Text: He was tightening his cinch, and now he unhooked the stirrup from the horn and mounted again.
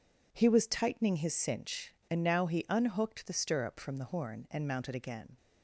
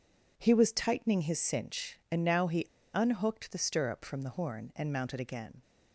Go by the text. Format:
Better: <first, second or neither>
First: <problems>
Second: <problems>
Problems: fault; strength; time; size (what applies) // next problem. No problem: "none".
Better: first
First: none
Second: pauses between "he" and "unhooked"; slight; at 2.6 s; 0.28 s long